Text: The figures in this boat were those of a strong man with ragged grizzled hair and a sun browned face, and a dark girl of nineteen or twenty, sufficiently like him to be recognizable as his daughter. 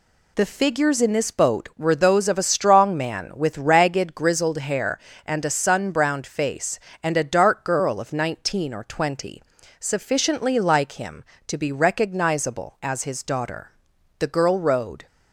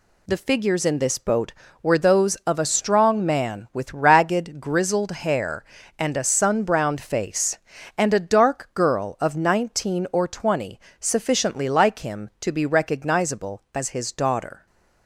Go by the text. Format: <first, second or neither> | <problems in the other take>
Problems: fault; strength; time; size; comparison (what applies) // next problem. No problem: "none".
second | goes on to say "The girl rowed"; noticeable; from 14.1 s on; 0.88 s long